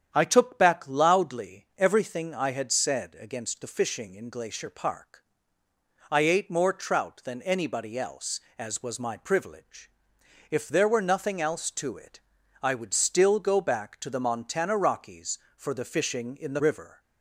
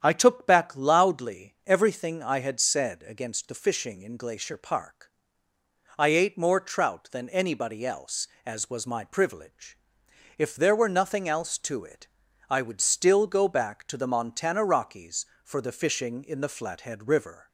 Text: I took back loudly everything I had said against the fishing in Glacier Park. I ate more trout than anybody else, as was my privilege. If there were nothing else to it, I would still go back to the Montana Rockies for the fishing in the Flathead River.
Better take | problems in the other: second | starts louder than the rest; strong; until 1.1 s; 9 dB; strong in the second // skips "Flathead"; at 16.6 s

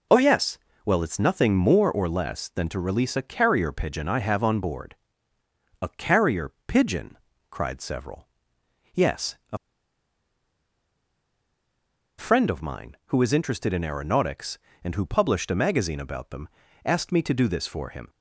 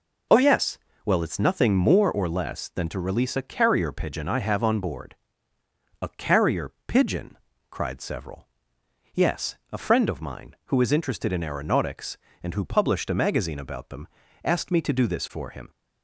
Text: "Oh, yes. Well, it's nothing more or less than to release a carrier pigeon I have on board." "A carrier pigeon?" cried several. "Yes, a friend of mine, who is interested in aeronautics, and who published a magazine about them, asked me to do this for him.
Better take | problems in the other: second | pauses between "a" and "friend"; strong; at 9.5 s; 2.6 s long

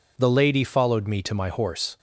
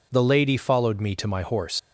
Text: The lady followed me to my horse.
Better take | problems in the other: first | leaves "horse" unfinished; at 1.7 s; 110 ms

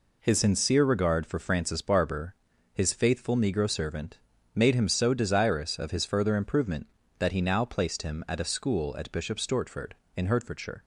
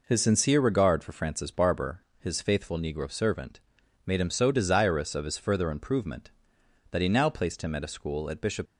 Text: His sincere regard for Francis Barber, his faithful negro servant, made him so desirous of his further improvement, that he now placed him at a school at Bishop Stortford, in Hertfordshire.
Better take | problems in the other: first | stops before "Stortford in Hertfordshire"; at 8.6 s

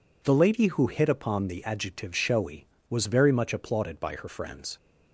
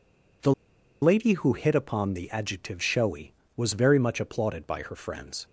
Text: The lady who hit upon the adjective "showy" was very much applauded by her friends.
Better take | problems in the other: first | pauses between "The" and "lady"; noticeable; at 0.5 s; 0.50 s long

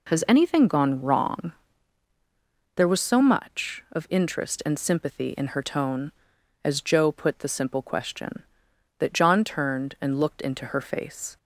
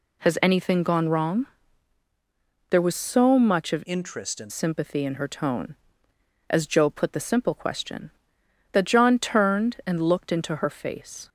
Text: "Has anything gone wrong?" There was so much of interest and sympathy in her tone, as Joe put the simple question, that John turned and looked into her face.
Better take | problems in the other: first | changes voice from "interest" to "and"; from 3.8 to 4.5 s; 0.7 s long

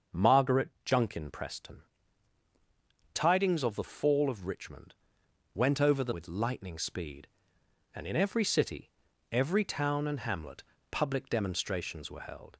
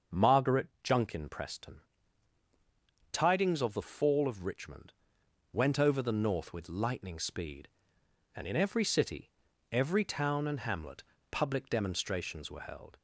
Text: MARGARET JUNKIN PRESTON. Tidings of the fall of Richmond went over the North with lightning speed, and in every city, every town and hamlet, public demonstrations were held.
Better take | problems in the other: second | starts louder than the rest; until 1.3 s; 6.5 dB; also in the second // pauses between "MARGARET" and "JUNKIN"; slight; at 0.6 s; 0.16 s long; slight in the second // pauses between "Richmond" and "went"; noticeable; at 4.9 s; 0.60 s long; noticeable in the second // skips "North"; at 6.1 s

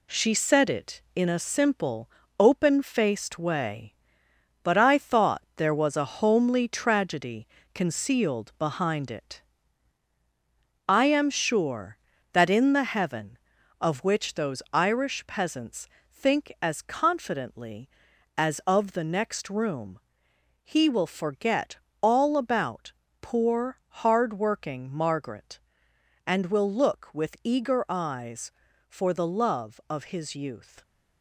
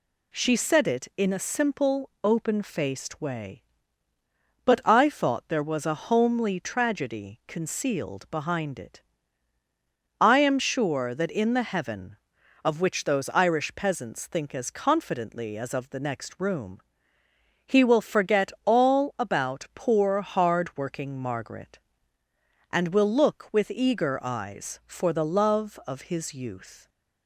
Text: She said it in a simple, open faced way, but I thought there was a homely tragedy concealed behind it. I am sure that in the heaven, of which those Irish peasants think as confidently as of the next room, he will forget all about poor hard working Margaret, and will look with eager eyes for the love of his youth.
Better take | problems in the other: second | gets quieter; noticeable; throughout; 5.5 dB // pauses between "tragedy" and "concealed"; slight; at 7.4 s; 0.30 s long // pauses between "peasants" and "think"; slight; at 15.8 s; 0.26 s long // pauses between "forget" and "all"; slight; at 21.7 s; 0.24 s long // pauses between "about" and "poor"; slight; at 22.9 s; 0.28 s long // pauses between "poor" and "hard"; slight; at 23.7 s; 0.24 s long

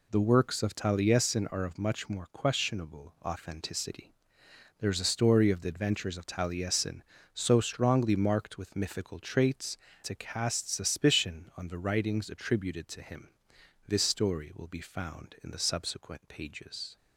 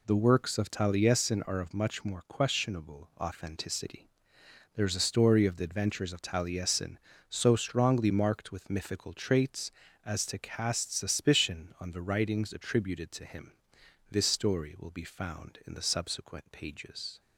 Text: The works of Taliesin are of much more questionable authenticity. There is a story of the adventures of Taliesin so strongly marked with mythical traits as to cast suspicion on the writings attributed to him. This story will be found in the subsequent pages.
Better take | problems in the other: second | skips "as"; at 9.9 s

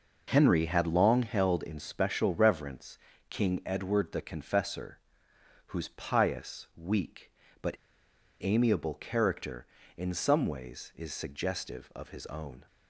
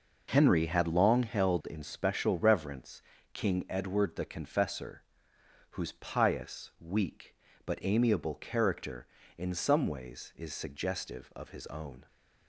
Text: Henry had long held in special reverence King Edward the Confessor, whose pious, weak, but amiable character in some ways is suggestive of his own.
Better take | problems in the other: second | pauses between "reverence" and "King"; slight; at 2.9 s; 0.32 s long; slight in the second // pauses between "but" and "amiable"; noticeable; at 7.7 s; 0.69 s long

